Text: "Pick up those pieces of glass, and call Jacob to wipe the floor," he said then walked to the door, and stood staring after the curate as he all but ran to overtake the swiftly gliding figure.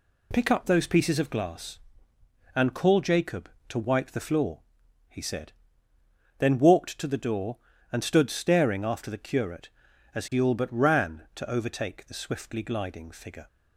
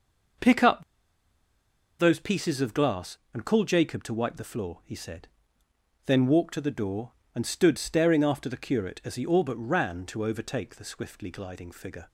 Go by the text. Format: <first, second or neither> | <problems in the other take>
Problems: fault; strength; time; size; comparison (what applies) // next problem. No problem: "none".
first | pauses between "up" and "those"; at 0.8 s; 1.1 s long // pauses between "said" and "then"; noticeable; at 5.2 s; 0.78 s long; noticeable in the first